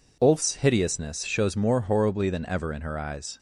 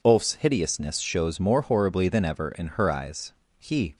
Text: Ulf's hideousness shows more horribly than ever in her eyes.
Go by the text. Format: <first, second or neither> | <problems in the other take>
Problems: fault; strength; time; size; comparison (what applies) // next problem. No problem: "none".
first | goes on to say "He"; slight; from 3.5 s on; 0.38 s long